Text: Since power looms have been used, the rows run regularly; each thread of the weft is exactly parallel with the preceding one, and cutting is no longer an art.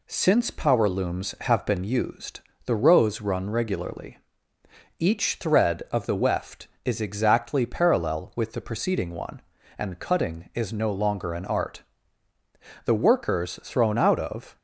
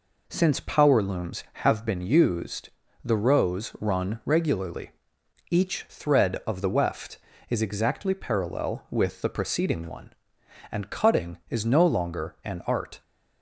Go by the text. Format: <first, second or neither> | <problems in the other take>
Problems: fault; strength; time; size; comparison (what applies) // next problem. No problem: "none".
second | goes on to say "The workers thrown out of"; strong; from 12.8 s on; 1.7 s long